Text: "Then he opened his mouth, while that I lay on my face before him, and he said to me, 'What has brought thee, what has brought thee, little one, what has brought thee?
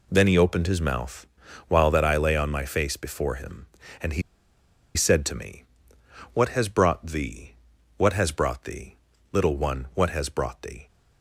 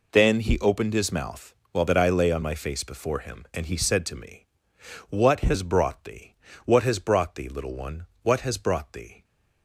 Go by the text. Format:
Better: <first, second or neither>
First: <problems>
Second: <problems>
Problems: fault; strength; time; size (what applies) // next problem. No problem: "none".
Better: second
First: pauses between "he" and "said"; noticeable; at 4.2 s; 0.73 s long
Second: none